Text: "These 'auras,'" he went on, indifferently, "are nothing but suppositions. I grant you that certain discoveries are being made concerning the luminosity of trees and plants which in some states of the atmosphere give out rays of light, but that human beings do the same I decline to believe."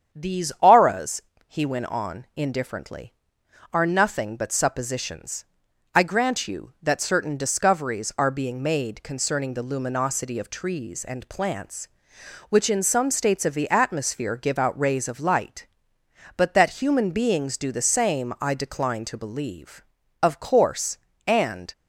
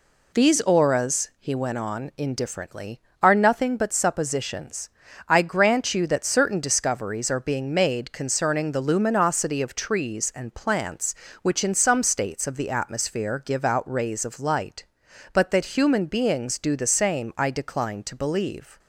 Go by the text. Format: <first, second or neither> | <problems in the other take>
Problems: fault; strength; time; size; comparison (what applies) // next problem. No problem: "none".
second | starts louder than the rest; strong; until 1.2 s; 8 dB // goes on to say "Of course and"; from 20.2 s on; 1.5 s long